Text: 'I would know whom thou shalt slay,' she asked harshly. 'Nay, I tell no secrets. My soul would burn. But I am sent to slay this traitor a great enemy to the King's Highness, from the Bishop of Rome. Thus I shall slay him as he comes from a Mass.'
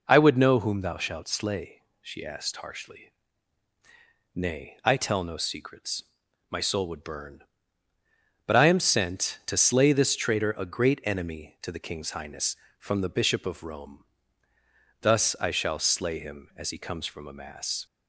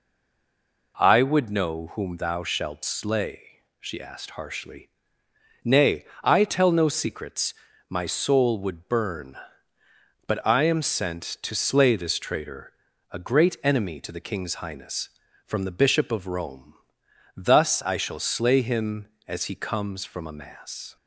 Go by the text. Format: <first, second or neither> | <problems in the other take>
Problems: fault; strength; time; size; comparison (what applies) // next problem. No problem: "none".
first | stays silent before the first word; slight; until 0.9 s; 0.9 s long // pauses between "traitor" and "a"; at 12.7 s; 0.40 s long